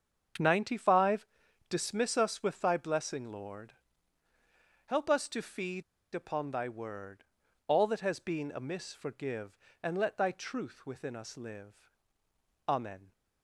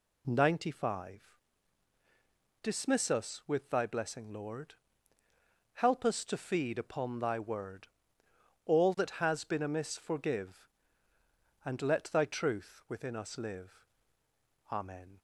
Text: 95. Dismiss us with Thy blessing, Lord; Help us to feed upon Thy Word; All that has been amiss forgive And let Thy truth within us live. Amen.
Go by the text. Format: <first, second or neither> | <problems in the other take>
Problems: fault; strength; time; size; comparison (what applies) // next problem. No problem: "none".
second | starts louder than the rest; strong; until 1.8 s; 7 dB // pauses between "feed" and "upon"; slight; at 5.8 s; 0.30 s long